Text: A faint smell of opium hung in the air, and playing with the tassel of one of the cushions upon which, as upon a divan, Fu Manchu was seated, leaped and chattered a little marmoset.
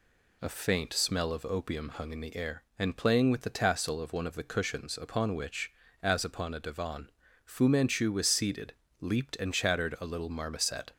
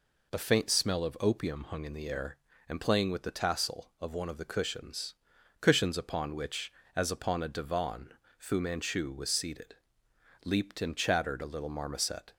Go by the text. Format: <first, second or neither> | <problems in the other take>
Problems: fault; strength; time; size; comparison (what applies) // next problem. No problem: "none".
first | says "cushions" twice; at 5.5 s